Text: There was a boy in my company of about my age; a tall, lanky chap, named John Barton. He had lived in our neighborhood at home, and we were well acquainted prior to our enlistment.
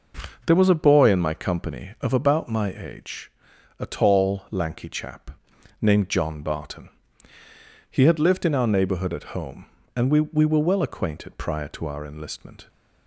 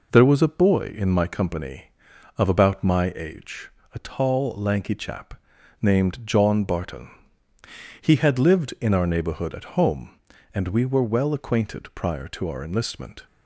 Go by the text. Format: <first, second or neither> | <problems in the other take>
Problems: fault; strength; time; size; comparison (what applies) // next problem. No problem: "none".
second | says "we" twice; at 10.2 s